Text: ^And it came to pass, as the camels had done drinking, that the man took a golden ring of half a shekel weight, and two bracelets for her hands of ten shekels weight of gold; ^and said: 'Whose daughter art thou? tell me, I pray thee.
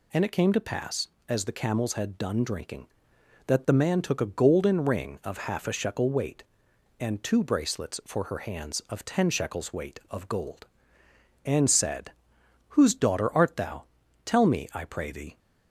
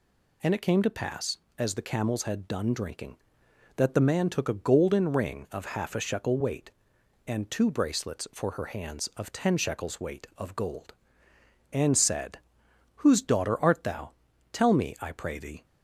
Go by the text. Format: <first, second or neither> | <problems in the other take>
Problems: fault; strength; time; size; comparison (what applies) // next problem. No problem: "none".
neither | none